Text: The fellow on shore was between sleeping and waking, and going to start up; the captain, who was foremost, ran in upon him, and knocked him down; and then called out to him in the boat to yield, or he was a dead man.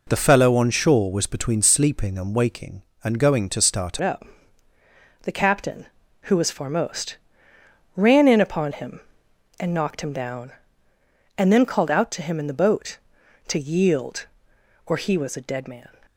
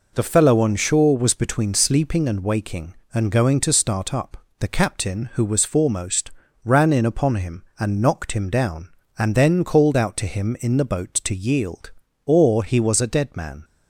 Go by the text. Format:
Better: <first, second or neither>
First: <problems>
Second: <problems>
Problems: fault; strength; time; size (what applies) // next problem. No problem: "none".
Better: second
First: changes voice at "up"; from 4.0 s on; 11.8 s long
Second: none